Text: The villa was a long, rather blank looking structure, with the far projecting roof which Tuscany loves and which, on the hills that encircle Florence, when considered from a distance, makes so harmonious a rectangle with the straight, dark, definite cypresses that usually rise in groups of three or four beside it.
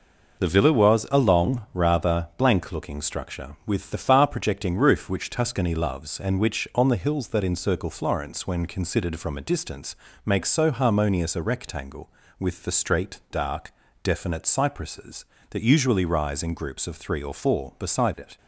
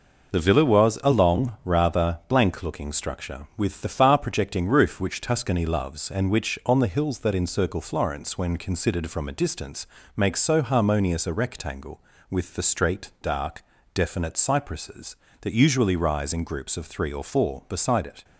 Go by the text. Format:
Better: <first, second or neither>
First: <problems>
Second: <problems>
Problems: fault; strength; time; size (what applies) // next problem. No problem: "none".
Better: neither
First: none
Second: none